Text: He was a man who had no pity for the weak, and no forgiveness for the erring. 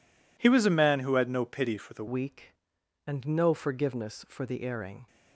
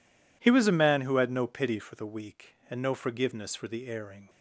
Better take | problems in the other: second | changes voice at "weak"; from 2.0 s on; 3.0 s long

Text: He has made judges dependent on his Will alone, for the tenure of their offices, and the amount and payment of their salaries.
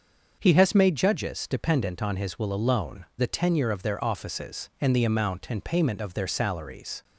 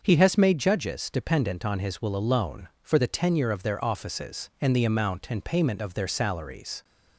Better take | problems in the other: second | starts louder than the rest; until 1.4 s; 6.5 dB; also in the second // skips "for"; at 3.1 s

